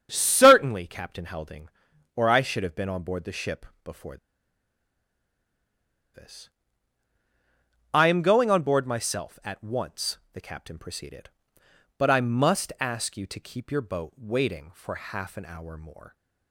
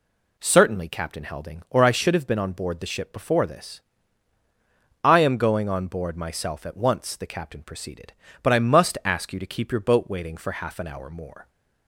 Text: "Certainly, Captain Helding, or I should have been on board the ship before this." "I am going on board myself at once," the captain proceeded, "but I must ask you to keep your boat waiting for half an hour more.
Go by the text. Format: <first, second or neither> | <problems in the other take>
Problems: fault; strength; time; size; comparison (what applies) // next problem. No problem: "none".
second | starts louder than the rest; strong; until 1.1 s; 8 dB // pauses between "ship" and "before"; slight; at 3.6 s; 0.20 s long // pauses between "before" and "this"; strong; at 4.1 s; 1.9 s long